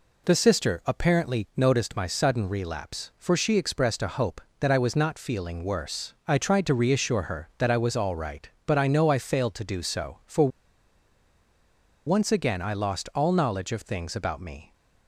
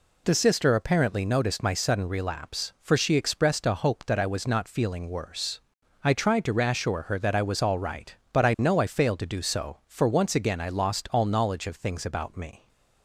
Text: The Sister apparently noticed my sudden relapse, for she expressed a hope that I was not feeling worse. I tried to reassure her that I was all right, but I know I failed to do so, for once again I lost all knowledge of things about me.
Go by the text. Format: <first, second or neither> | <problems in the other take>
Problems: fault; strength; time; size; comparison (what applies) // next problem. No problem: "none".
second | pauses between "for" and "once"; strong; at 10.4 s; 1.5 s long